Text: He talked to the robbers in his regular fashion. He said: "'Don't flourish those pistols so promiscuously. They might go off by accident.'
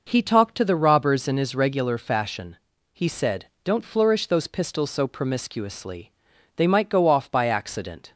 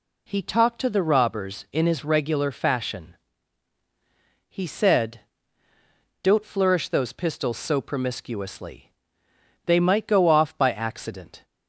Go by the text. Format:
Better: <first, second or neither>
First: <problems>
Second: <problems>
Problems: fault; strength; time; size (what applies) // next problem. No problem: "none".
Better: neither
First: none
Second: none